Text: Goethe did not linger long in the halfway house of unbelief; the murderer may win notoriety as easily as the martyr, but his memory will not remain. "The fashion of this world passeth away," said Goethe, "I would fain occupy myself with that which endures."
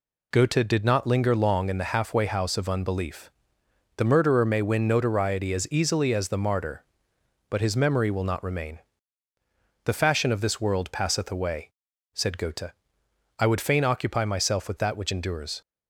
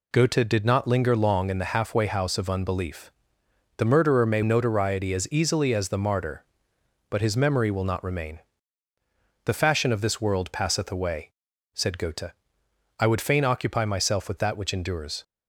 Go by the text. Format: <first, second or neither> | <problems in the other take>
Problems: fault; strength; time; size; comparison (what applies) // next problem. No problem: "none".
first | skips "win"; at 4.4 s